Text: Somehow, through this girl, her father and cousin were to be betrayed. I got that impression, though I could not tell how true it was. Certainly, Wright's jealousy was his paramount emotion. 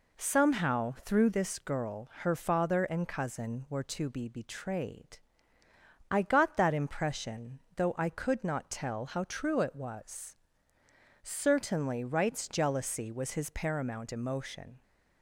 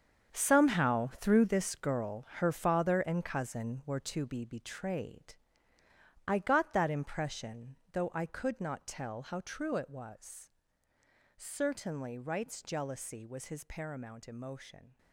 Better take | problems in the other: first | gets quieter; strong; throughout; 12.5 dB

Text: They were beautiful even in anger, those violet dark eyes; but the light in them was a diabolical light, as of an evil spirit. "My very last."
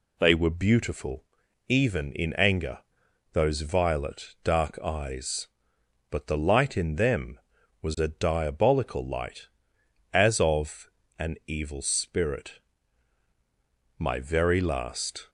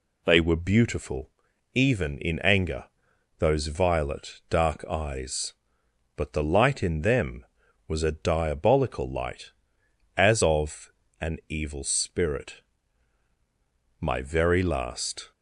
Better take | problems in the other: neither | pauses between "beautiful" and "even"; noticeable; the same in both // pauses between "of" and "an"; slight; the same in both

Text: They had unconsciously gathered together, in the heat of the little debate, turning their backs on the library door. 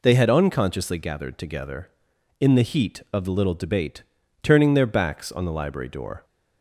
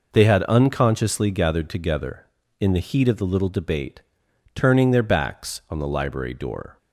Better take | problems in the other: neither | none

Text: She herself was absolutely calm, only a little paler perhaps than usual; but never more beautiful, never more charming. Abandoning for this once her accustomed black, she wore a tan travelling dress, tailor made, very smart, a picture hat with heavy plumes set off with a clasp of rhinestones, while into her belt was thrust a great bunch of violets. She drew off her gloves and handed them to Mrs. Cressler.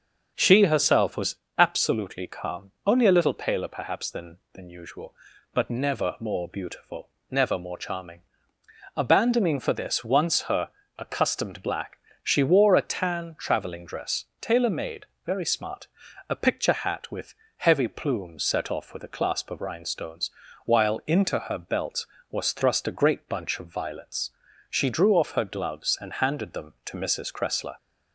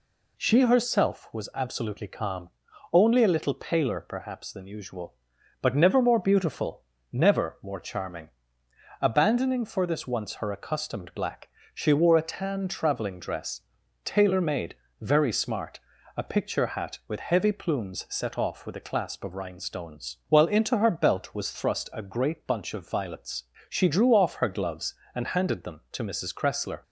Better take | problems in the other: second | pauses between "was" and "absolutely"; slight; at 1.3 s; 0.22 s long // says "than" twice; at 4.5 s // pauses between "her" and "accustomed"; slight; at 10.7 s; 0.26 s long // pauses between "with" and "heavy"; slight; at 17.3 s; 0.22 s long

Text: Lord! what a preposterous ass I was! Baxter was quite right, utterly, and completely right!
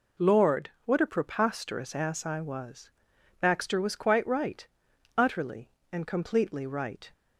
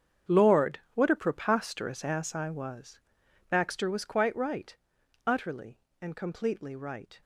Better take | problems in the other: first | gets quieter; strong; throughout; 15 dB

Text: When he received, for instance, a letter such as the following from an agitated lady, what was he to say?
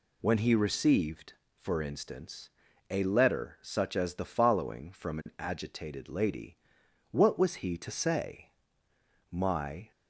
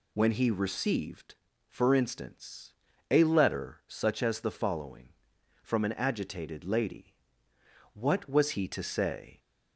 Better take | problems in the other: second | goes on to say "MY"; from 9.3 s on; 0.60 s long

